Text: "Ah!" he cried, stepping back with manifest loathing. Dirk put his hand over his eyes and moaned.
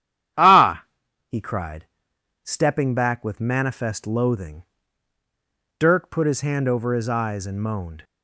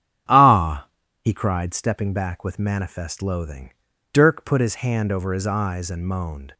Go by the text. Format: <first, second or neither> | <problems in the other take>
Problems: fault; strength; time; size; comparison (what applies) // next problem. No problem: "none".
neither | starts louder than the rest; strong; the same in both